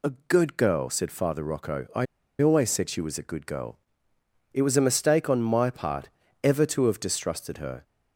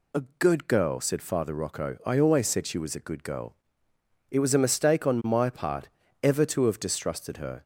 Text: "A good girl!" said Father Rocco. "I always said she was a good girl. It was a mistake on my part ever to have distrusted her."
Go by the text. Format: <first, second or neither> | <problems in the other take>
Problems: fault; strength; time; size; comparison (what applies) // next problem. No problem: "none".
second | pauses between "A" and "good"; slight; at 0.1 s; 0.16 s long; slight in the second // pauses between "I" and "always"; slight; at 2.0 s; 0.35 s long // pauses between "part" and "ever"; slight; at 6.0 s; 0.32 s long; slight in the second